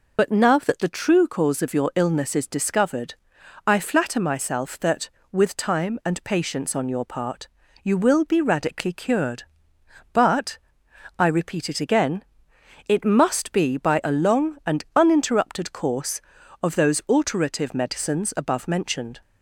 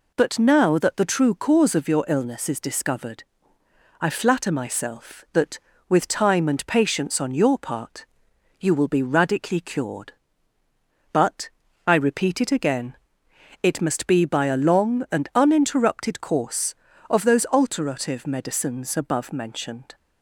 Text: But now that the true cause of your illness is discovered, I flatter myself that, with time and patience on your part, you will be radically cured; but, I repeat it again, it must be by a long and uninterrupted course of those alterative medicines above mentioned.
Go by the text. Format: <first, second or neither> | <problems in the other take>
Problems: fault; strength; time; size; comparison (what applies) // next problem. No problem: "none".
second | loses the start of "But"; at 0.1 s; 45 ms